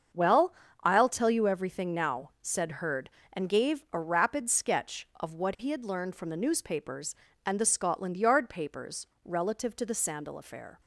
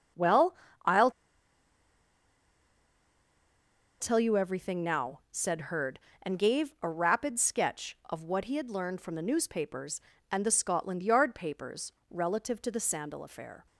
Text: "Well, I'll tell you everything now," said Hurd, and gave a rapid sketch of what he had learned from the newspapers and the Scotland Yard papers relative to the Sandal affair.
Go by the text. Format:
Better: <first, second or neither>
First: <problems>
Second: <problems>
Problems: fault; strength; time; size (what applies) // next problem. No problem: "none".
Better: first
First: starts louder than the rest; until 1.4 s; 7 dB // pauses between "papers" and "relative"; slight; at 9.0 s; 0.18 s long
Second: starts louder than the rest; until 4.3 s; 7 dB // pauses between "I'll" and "tell"; strong; at 1.0 s; 2.9 s long // pauses between "papers" and "relative"; slight; at 11.9 s; 0.18 s long